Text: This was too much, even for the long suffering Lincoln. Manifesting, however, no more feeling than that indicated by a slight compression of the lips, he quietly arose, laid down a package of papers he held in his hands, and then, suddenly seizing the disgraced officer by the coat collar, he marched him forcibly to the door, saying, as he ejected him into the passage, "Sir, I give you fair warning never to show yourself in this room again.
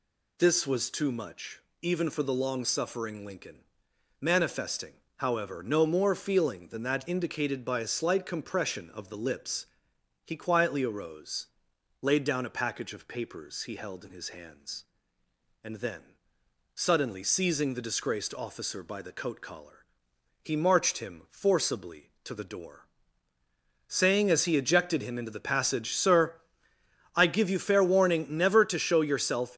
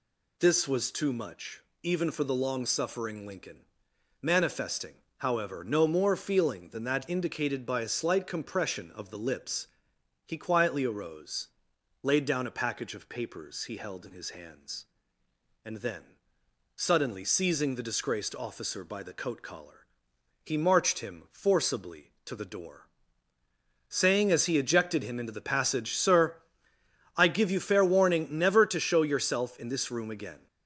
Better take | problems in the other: second | stops before "in this room again"; at 29.5 s

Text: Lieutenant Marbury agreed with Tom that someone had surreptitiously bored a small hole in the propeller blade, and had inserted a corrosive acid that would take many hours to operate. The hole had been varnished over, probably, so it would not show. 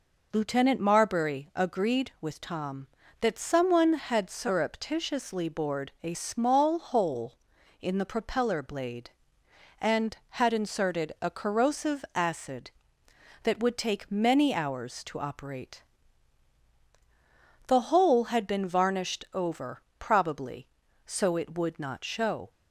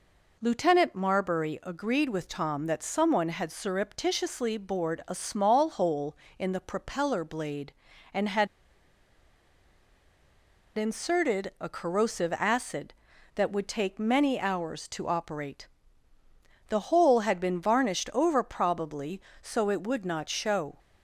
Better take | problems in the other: first | pauses between "had" and "inserted"; strong; at 8.4 s; 2.2 s long

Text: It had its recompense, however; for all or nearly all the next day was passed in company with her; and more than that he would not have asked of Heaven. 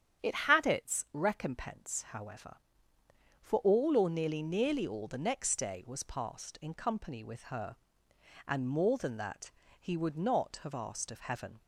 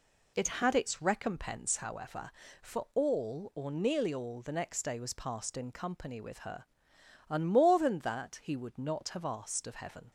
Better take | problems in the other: second | starts louder than the rest; strong; until 1.3 s; 9 dB // says "nearly" twice; at 4.4 s // pauses between "that" and "he"; slight; at 9.4 s; 0.30 s long

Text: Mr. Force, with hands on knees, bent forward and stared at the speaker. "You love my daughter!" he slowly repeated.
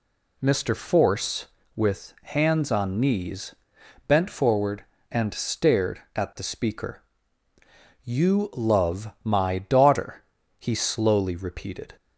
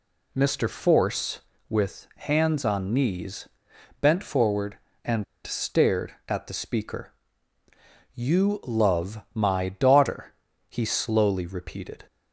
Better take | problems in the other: first | pauses between "and" and "stared"; slight; at 5.2 s; 0.21 s long

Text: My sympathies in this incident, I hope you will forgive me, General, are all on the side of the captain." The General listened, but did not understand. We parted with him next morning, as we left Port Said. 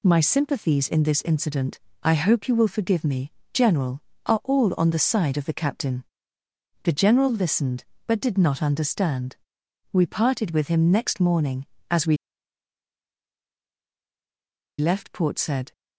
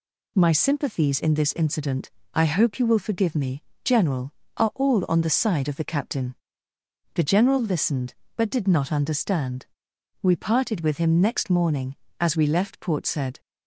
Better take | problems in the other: second | pauses between "we" and "left"; strong; at 12.1 s; 2.6 s long

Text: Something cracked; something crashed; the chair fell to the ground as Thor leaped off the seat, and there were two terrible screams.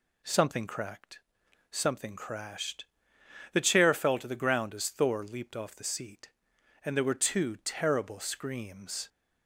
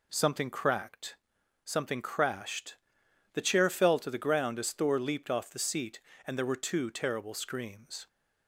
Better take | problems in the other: neither | none

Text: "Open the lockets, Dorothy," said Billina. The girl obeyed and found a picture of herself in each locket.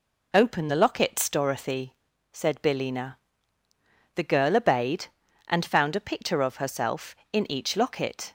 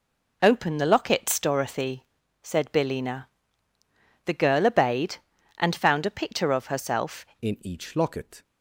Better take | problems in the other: first | changes voice at "in"; from 7.4 s on; 1.0 s long

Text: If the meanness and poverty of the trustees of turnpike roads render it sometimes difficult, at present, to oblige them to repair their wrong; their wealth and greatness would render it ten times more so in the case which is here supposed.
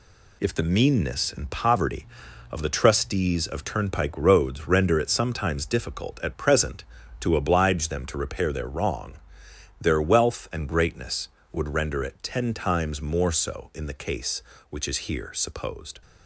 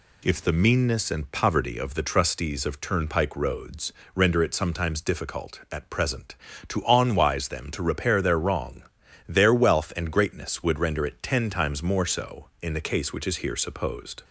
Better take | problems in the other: first | pauses between "roads" and "render"; slight; at 3.9 s; 0.24 s long // says "onwise" for "oblige"; at 6.8 s

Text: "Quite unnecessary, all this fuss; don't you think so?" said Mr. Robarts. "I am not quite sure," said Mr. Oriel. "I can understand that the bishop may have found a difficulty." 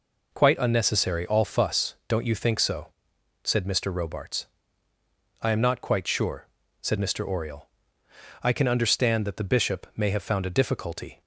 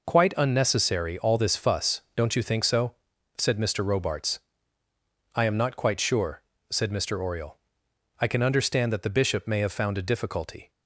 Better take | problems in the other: second | skips "this"; at 1.4 s

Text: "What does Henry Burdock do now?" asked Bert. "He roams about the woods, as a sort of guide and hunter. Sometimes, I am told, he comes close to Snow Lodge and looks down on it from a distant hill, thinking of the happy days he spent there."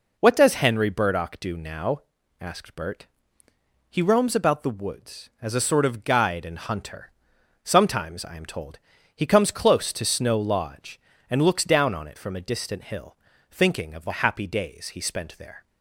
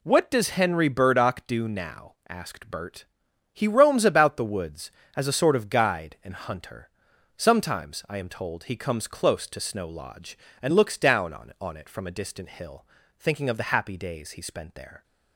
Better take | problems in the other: first | says "on" twice; at 11.5 s

